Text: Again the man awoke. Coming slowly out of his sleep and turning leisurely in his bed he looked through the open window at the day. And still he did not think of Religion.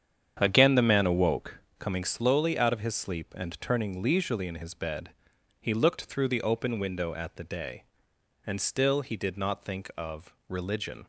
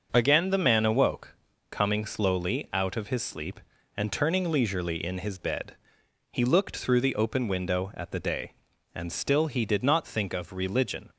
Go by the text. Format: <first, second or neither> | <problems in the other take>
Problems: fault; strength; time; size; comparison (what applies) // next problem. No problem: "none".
second | starts louder than the rest; strong; until 1.6 s; 8.5 dB // pauses between "bed" and "he"; noticeable; at 5.0 s; 0.50 s long; noticeable in the second // pauses between "of" and "Religion"; slight; at 10.3 s; 0.16 s long